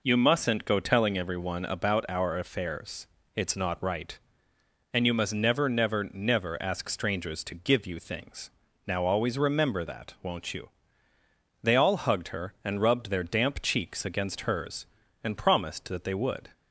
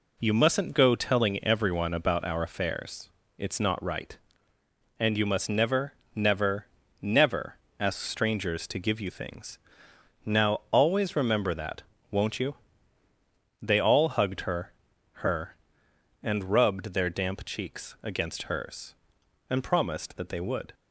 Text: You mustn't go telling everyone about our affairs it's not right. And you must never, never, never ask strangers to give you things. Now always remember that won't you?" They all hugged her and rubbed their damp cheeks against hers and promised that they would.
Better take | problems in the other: first | pauses between "affairs" and "it's"; slight; at 3.0 s; 0.28 s long; slight in the first // pauses between "never" and "ask"; slight; at 7.5 s; 0.22 s long // pauses between "that" and "won't"; slight; at 11.8 s; 0.26 s long // says "her" twice; at 15.2 s

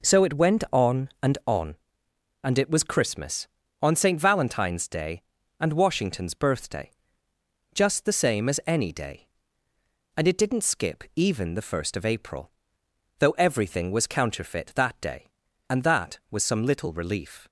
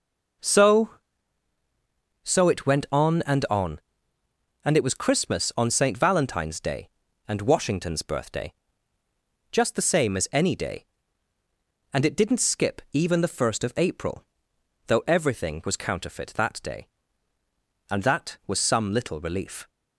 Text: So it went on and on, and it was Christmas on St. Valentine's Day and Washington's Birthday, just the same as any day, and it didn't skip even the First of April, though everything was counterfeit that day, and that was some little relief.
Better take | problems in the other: first | says "So" twice; at 2.2 s

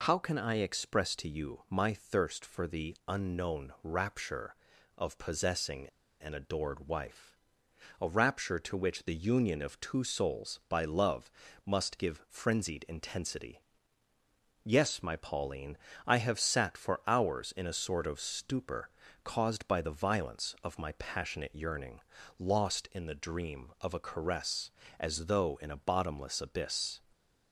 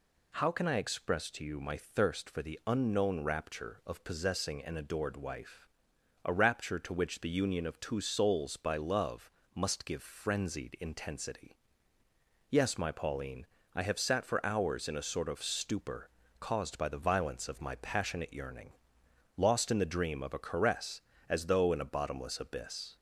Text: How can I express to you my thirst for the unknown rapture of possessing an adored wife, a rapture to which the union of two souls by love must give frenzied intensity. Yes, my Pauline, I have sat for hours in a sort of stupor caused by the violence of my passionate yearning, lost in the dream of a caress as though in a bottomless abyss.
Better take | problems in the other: second | pauses between "possessing" and "an"; at 5.8 s; 0.36 s long // pauses between "love" and "must"; slight; at 11.3 s; 0.36 s long; slight in the second // pauses between "stupor" and "caused"; slight; at 18.8 s; 0.36 s long; slight in the second

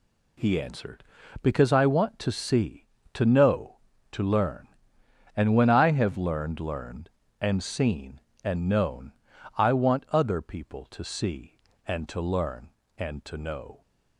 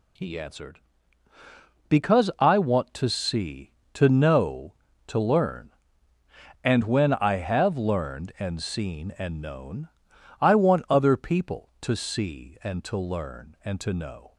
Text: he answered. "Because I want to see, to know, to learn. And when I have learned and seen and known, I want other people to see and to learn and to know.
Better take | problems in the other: second | says "learned" twice; at 6.5 s

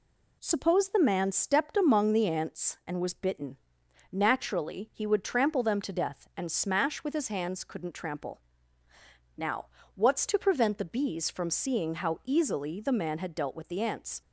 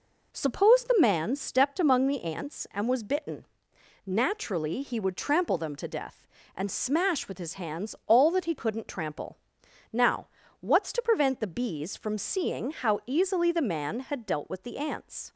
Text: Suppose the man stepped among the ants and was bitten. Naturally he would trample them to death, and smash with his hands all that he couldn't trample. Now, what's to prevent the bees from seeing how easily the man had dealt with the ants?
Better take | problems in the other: second | skips "all that he"; at 7.6 s

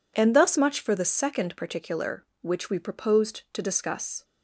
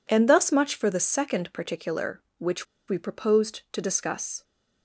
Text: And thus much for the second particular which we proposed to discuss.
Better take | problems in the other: first | pauses between "which" and "we"; slight; at 2.6 s; 0.23 s long

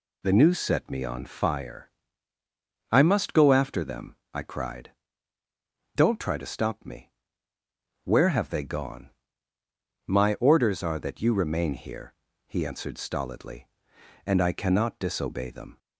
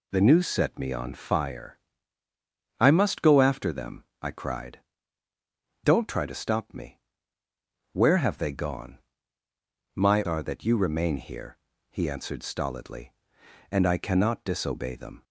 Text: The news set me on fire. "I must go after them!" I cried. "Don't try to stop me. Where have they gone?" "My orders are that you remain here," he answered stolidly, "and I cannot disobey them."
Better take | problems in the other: first | skips "orders"; at 10.2 s

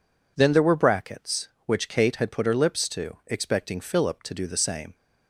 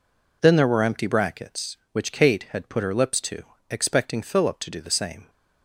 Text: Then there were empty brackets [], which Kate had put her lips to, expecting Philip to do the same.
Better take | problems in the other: second | skips "empty"; at 0.7 s

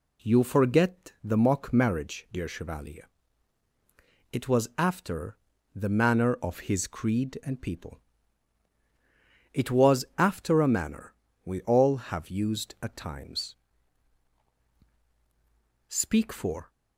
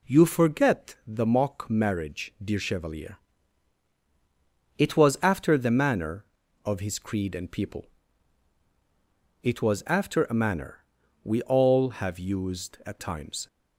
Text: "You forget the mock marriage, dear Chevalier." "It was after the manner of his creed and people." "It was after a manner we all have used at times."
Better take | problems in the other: second | pauses between "after" and "the"; slight; at 5.3 s; 0.36 s long // pauses between "manner" and "we"; slight; at 11.1 s; 0.32 s long; also in the second // goes on to say "Speak for"; noticeable; from 15.8 s on; 0.82 s long

